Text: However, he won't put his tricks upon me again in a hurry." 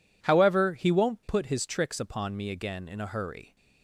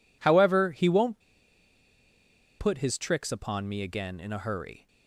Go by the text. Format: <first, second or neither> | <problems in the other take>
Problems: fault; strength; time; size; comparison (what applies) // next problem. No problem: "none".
first | pauses between "won't" and "put"; strong; at 1.2 s; 1.3 s long